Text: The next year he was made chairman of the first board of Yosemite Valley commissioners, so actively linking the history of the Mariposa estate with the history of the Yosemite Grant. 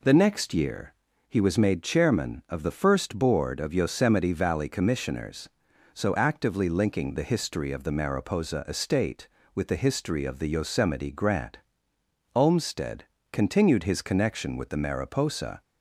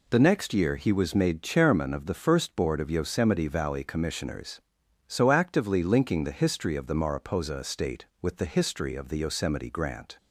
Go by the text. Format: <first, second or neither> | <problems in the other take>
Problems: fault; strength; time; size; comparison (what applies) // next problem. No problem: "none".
second | pauses between "year" and "he"; slight; at 0.9 s; 0.36 s long // goes on to say "Olmsted continued his connection with the Mariposa"; strong; from 12.3 s on; 3.2 s long